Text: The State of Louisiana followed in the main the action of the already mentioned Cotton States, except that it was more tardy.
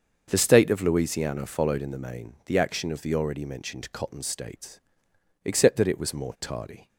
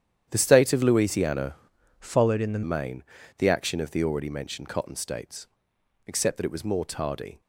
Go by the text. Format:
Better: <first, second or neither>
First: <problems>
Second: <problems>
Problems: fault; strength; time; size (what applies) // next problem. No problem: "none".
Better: first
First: starts louder than the rest; until 1.3 s; 6.5 dB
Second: starts louder than the rest; strong; until 1.3 s; 10 dB // changes voice from "followed" to "the"; from 1.9 to 2.6 s; 0.7 s long // pauses between "main" and "the"; slight; at 3.0 s; 0.36 s long